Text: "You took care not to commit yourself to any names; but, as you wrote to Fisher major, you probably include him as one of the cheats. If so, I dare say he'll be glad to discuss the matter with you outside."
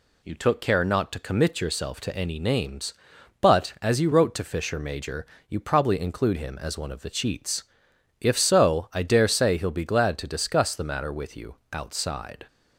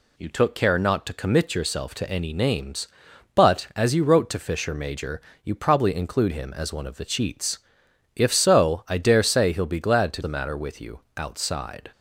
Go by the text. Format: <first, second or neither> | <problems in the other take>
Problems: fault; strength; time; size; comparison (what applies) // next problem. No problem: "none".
first | skips "discuss"; at 10.2 s // pauses between "you" and "outside"; slight; at 10.9 s; 0.16 s long; slight in the first